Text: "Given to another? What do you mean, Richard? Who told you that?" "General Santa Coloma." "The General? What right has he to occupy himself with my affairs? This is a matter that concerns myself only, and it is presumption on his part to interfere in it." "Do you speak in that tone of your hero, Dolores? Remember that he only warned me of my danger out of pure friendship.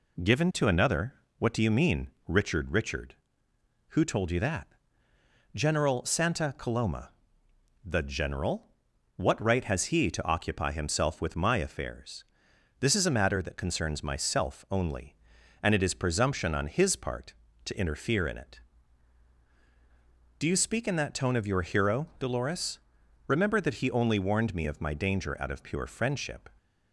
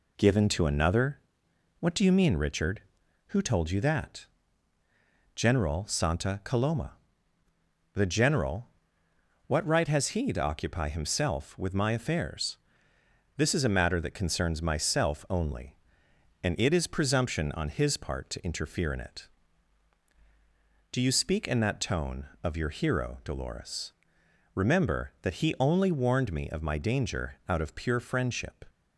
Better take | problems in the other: second | says "Richard" twice; at 2.7 s

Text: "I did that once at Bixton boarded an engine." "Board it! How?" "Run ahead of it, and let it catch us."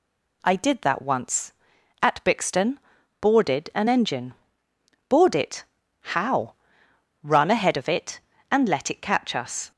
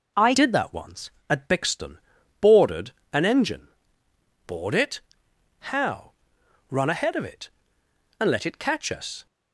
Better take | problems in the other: first | changes voice at "did"; from 0.3 s on; 8.9 s long // pauses between "Bixton" and "boarded"; at 1.9 s; 0.40 s long; also in the first // pauses between "boarded" and "an"; slight; at 2.8 s; 0.24 s long

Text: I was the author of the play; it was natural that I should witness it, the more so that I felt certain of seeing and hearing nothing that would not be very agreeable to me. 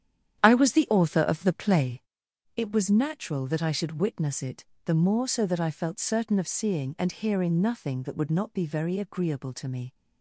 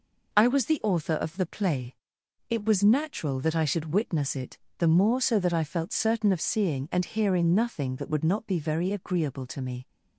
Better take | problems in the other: second | starts louder than the rest; strong; until 2.1 s; 10 dB

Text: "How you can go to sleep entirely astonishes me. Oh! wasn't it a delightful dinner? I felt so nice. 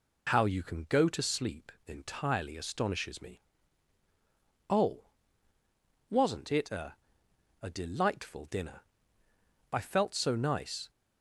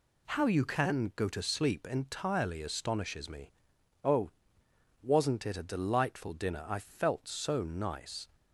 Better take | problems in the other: second | says "a" twice; at 7.6 s

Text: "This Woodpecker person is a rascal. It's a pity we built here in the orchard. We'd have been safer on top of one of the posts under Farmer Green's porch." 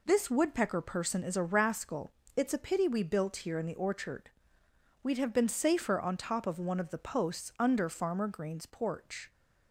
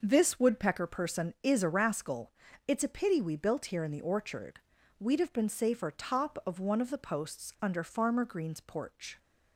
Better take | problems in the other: first | skips "on"; at 5.9 s

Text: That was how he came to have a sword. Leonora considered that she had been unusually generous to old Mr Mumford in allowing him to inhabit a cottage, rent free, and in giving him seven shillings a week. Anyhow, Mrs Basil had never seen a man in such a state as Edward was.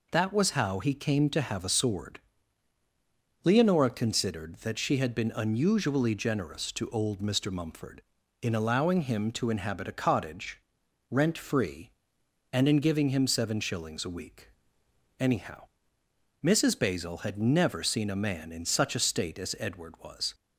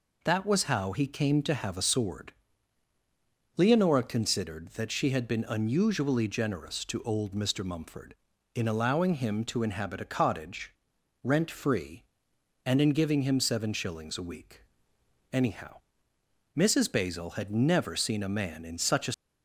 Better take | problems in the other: first | stops before "state as Edward was"; at 19.1 s

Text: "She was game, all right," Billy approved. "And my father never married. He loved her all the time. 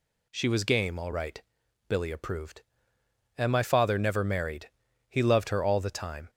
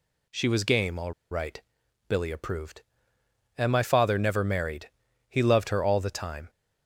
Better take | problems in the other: first | pauses between "all" and "right"; slight; at 1.1 s; 0.18 s long

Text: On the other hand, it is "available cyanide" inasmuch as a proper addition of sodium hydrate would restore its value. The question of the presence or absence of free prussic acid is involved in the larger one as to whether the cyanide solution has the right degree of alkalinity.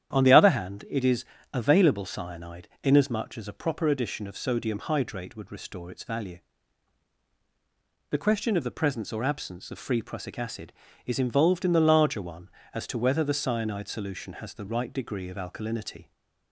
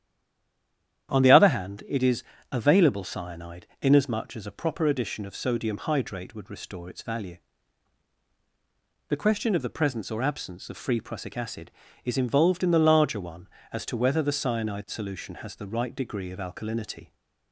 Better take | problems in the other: first | stays silent before the first word; until 1.0 s; 1.0 s long // starts louder than the rest; strong; until 2.1 s; 10 dB; strong in the first // pauses between "is" and "available"; slight; at 2.2 s; 0.30 s long; slight in the first // pauses between "cyanide" and "inasmuch"; slight; at 3.6 s; 0.16 s long; slight in the first

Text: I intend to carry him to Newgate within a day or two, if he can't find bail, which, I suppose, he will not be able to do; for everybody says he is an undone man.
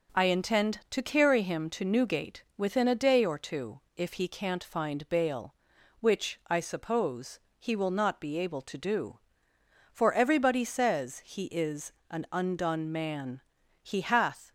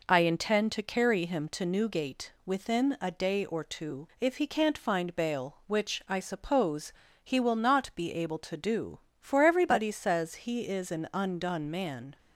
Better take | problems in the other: second | pauses between "is" and "an"; slight; at 11.9 s; 0.16 s long // goes on to say "He hath"; noticeable; from 13.8 s on; 0.68 s long

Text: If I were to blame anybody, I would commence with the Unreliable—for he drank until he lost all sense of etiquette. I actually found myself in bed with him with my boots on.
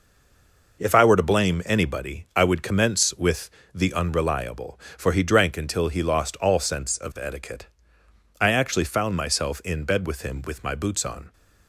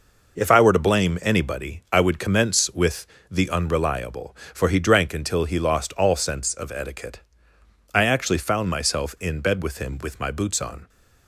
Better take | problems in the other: second | stays silent before the first word; slight; until 0.7 s; 0.7 s long // pauses between "with" and "the"; slight; at 3.4 s; 0.24 s long; slight in the second

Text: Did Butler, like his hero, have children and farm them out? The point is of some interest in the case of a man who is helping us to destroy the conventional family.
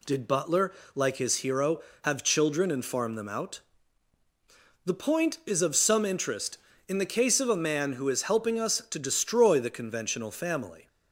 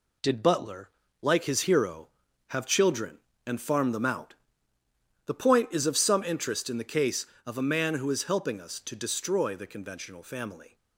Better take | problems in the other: first | gets quieter; noticeable; throughout; 5.5 dB

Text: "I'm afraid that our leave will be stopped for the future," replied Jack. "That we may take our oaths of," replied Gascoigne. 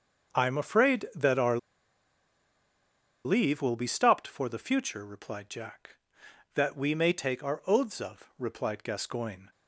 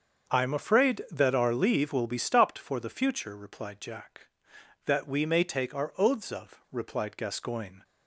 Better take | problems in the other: second | starts louder than the rest; until 1.3 s; 6.5 dB; also in the second // pauses between "our" and "leave"; strong; at 1.5 s; 1.6 s long

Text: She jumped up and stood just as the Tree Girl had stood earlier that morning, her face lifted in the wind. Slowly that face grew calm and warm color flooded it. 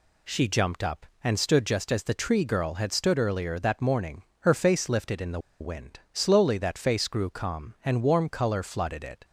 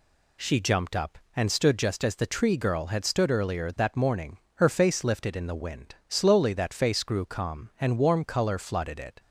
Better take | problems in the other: second | pauses between "the" and "wind"; slight; at 5.3 s; 0.21 s long

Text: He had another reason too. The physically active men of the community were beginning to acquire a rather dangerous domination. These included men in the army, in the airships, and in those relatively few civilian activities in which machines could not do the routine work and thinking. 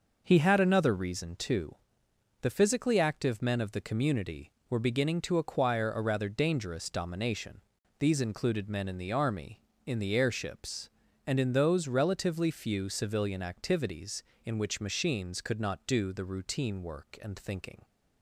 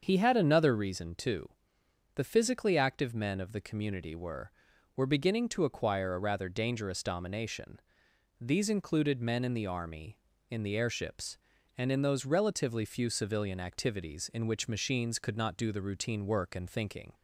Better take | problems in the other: first | starts louder than the rest; until 1.0 s; 6.5 dB // says "were" twice; at 4.9 s

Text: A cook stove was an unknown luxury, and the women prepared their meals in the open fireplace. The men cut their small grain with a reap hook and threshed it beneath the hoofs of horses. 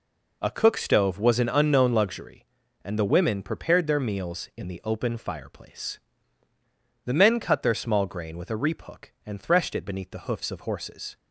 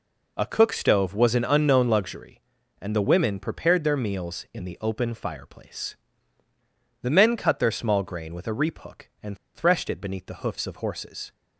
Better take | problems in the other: first | pauses between "and" and "threshed"; slight; at 9.3 s; 0.18 s long

